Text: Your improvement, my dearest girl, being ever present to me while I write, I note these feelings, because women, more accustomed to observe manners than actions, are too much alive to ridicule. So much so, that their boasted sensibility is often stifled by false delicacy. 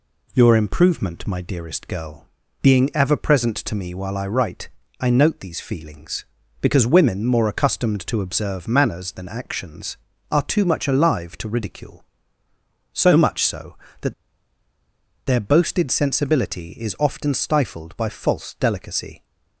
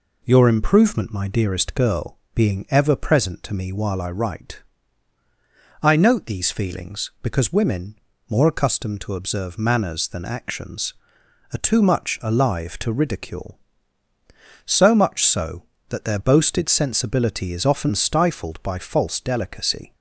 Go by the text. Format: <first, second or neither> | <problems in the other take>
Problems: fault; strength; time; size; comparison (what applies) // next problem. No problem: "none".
second | pauses between "that" and "their"; at 14.1 s; 1.1 s long